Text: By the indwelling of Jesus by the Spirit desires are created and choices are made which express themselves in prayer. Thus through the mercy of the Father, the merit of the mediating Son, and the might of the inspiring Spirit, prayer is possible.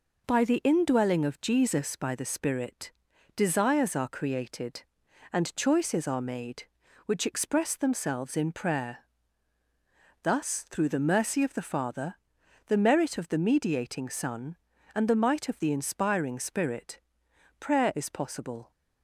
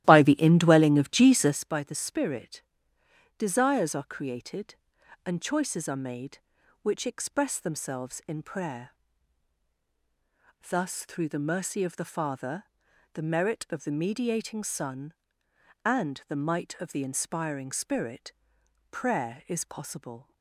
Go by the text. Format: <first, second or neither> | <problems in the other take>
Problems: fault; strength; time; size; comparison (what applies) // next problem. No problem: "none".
first | starts louder than the rest; strong; until 1.6 s; 14 dB // pauses between "Spirit" and "desires"; noticeable; at 2.6 s; 0.78 s long; noticeable in the first